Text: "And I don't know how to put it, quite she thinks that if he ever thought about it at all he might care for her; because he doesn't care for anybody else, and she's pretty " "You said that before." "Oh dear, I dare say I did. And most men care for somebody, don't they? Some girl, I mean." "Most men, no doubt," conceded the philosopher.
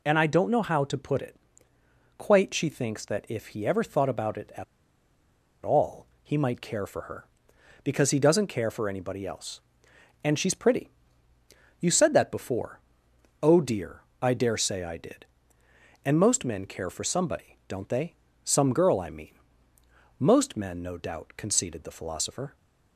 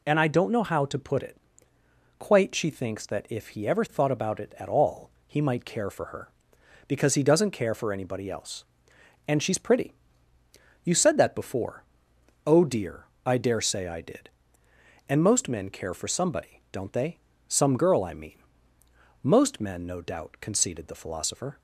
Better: second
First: pauses between "at" and "all"; at 4.6 s; 1.0 s long // pauses between "all" and "he"; slight; at 6.0 s; 0.16 s long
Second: pauses between "all" and "he"; slight; at 5.1 s; 0.16 s long

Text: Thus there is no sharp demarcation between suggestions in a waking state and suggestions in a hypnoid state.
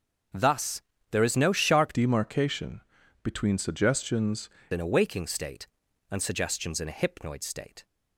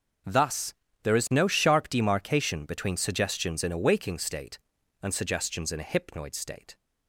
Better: second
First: starts louder than the rest; until 1.6 s; 7 dB // pauses between "Thus" and "there"; slight; at 0.8 s; 0.28 s long // changes voice from "demarcation" to "suggestions"; from 1.9 to 4.4 s; 2.5 s long // pauses between "demarcation" and "between"; at 2.8 s; 0.42 s long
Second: starts louder than the rest; until 1.6 s; 6.5 dB // pauses between "Thus" and "there"; slight; at 0.7 s; 0.28 s long

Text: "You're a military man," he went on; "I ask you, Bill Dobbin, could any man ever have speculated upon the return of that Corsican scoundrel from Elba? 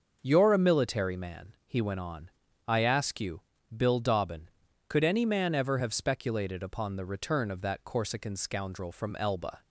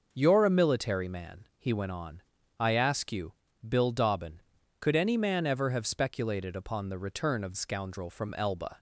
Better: first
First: starts louder than the rest; until 1.2 s; 6 dB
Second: starts louder than the rest; noticeable; until 1.1 s; 6 dB // skips "that Corsican"; at 7.5 s

